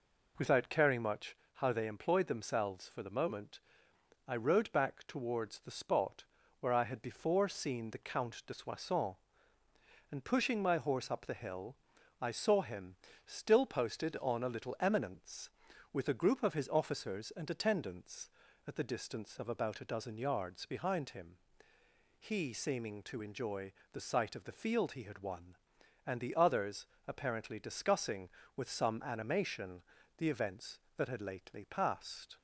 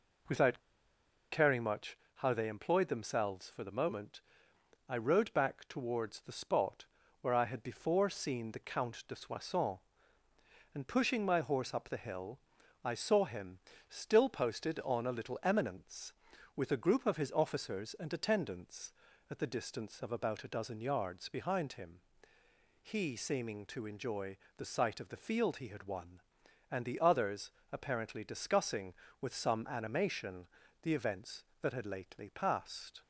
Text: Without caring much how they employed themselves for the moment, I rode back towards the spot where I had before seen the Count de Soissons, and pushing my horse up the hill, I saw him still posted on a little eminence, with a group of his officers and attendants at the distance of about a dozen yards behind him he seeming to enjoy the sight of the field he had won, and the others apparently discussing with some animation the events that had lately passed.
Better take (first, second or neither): first